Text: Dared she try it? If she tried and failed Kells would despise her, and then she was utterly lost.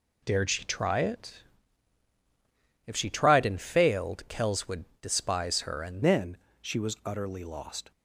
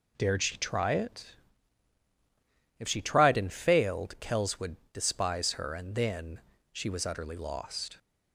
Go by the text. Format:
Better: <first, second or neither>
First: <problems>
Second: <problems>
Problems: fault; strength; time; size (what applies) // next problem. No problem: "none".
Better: second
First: pauses between "would" and "despise"; slight; at 4.8 s; 0.16 s long // changes voice at "then"; from 6.0 s on; 1.9 s long // pauses between "then" and "she"; slight; at 6.3 s; 0.22 s long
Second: pauses between "would" and "despise"; slight; at 4.7 s; 0.16 s long // pauses between "then" and "she"; slight; at 6.3 s; 0.32 s long